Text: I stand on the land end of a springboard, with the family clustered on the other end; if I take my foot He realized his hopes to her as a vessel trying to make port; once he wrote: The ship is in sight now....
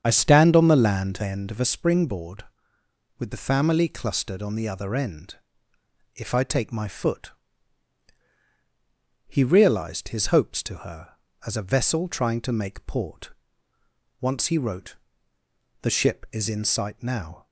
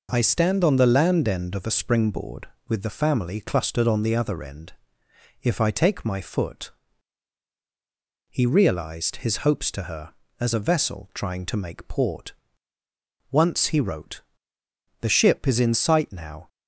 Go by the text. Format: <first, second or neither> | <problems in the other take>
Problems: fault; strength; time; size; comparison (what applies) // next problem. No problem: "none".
second | starts louder than the rest; strong; until 1.7 s; 7.5 dB // pauses between "foot" and "He"; strong; at 7.3 s; 1.9 s long; strong in the second